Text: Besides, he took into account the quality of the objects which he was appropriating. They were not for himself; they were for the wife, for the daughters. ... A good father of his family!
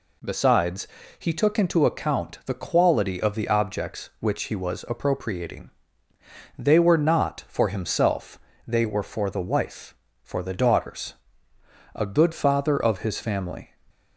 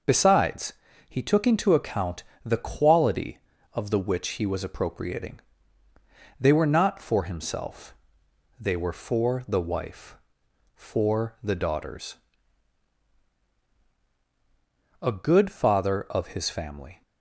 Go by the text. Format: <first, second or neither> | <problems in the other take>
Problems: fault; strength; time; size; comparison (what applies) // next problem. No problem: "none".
first | pauses between "account" and "the"; slight; at 2.2 s; 0.20 s long // skips "objects"; at 3.9 s